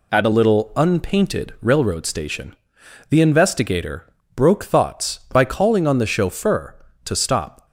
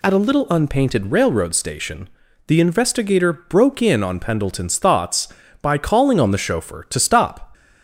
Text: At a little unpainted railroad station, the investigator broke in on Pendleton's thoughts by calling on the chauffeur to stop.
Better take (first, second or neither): second